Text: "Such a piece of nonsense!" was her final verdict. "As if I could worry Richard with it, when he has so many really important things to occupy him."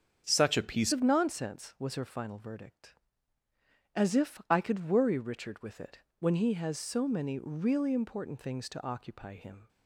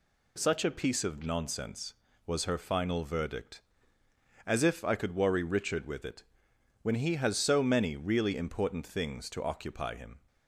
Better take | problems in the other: second | starts louder than the rest; strong; until 1.2 s; 7 dB // changes voice at "of"; from 0.9 s on; 8.7 s long

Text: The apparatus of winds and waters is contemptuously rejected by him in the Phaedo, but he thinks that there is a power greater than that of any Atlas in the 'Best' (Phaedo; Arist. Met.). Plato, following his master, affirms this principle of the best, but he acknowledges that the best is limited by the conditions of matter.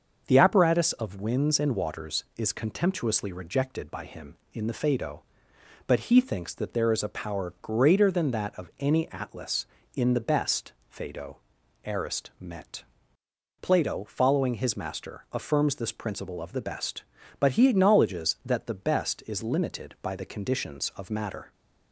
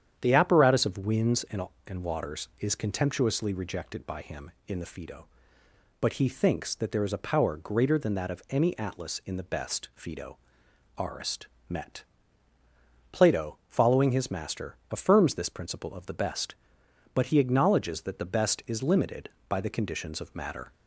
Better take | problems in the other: first | starts louder than the rest; strong; until 1.2 s; 9 dB; also in the first // says "and" twice; at 1.8 s

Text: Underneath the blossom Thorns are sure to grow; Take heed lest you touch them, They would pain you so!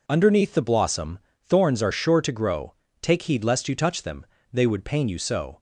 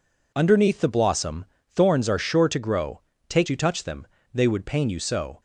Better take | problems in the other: first | pauses between "blossom" and "Thorns"; slight; at 1.4 s; 0.24 s long; slight in the first // skips "heed lest"; at 3.4 s

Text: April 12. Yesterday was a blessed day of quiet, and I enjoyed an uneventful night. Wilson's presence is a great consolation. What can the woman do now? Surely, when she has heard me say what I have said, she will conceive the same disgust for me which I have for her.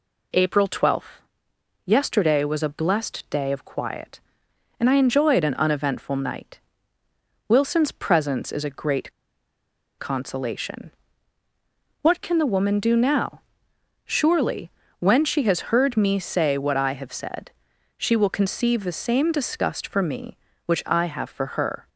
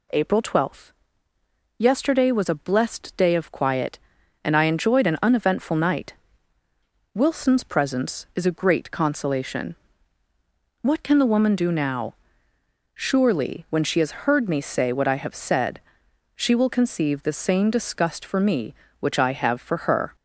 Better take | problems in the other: second | pauses between "great" and "consolation"; noticeable; at 9.1 s; 0.86 s long

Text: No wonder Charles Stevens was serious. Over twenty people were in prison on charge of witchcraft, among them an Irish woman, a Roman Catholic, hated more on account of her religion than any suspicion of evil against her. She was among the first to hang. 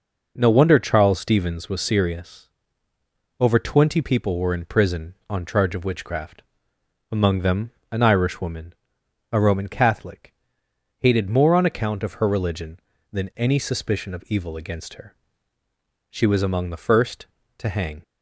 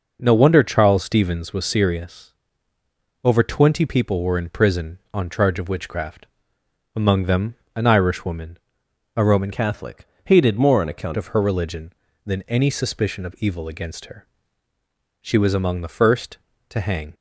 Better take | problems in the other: first | pauses between "them" and "an"; slight; at 7.5 s; 0.20 s long; slight in the first // changes voice from "Catholic" to "account"; from 9.5 to 11.1 s; 1.6 s long

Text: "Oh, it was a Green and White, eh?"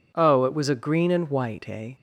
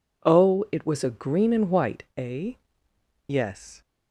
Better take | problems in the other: first | goes on to say "Yes"; from 3.2 s on; 0.54 s long

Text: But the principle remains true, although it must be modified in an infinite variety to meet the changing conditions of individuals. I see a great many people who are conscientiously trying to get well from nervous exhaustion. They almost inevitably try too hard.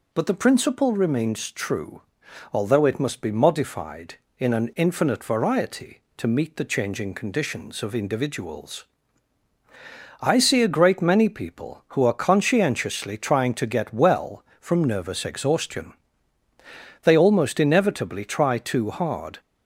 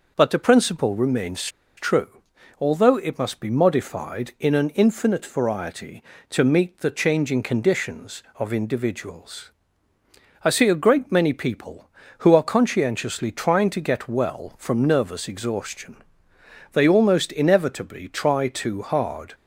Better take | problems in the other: first | pauses between "remains" and "true"; slight; at 1.4 s; 0.33 s long

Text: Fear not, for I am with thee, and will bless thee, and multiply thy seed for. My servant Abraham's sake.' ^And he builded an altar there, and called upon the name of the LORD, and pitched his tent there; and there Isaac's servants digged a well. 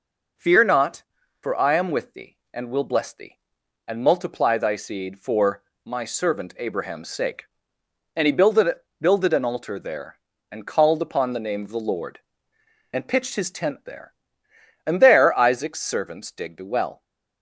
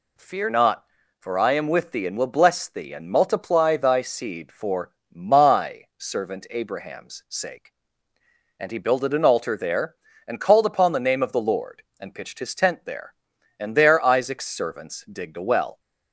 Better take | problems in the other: second | says "builded" twice; at 8.9 s

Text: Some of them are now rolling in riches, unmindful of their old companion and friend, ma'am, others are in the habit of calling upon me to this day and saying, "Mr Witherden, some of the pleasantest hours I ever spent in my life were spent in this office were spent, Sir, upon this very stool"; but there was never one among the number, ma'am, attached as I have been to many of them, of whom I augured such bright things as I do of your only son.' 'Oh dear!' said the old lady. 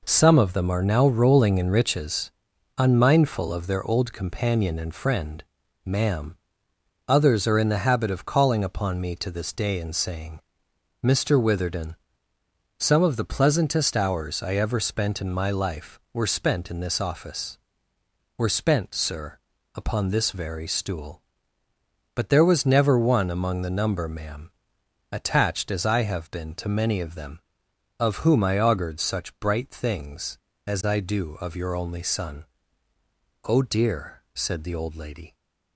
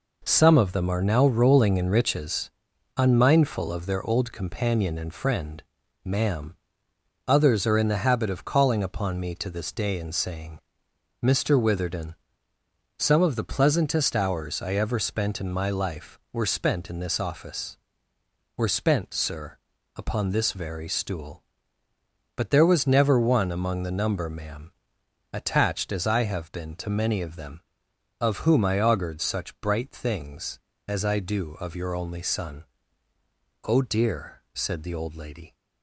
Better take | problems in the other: neither | none

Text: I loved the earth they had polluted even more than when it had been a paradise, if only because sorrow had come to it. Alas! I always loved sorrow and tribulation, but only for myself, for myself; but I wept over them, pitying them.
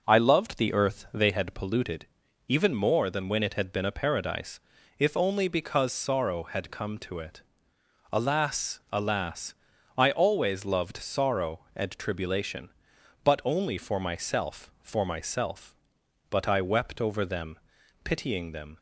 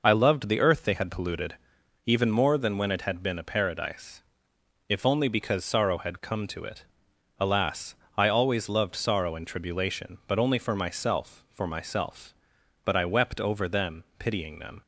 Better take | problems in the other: second | pauses between "polluted" and "even"; at 2.0 s; 0.40 s long; noticeable in the second // says "Alas" twice; at 8.8 s

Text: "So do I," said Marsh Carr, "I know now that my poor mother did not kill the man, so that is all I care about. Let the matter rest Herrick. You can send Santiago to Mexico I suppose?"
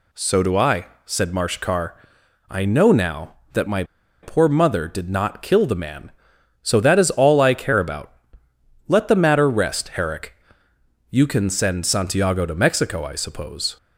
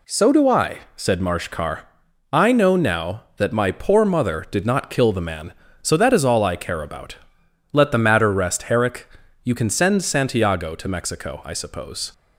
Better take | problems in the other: second | pauses between "my" and "poor"; at 3.8 s; 0.39 s long

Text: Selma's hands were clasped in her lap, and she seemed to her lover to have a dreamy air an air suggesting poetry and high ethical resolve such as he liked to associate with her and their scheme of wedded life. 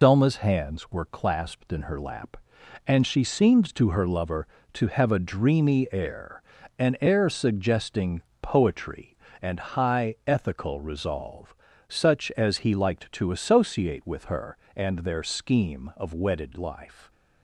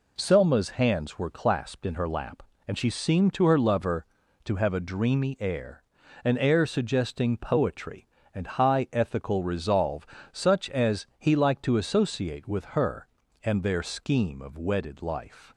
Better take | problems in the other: second | loses the start of "Selma's"; at 0.0 s; 110 ms // pauses between "air" and "an"; at 6.4 s; 0.38 s long; also in the second // pauses between "suggesting" and "poetry"; slight; at 8.2 s; 0.18 s long // pauses between "resolve" and "such"; slight; at 11.5 s; 0.34 s long; slight in the second

